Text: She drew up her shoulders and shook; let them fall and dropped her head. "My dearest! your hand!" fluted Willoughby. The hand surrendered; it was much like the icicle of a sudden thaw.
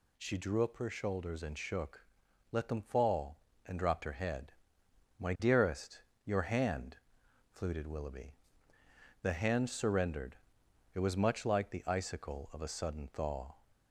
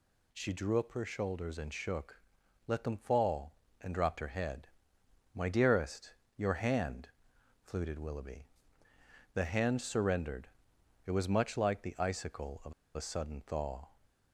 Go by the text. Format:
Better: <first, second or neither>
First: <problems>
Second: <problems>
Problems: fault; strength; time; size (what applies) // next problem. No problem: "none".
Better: first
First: none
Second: pauses between "of" and "a"; slight; at 12.7 s; 0.22 s long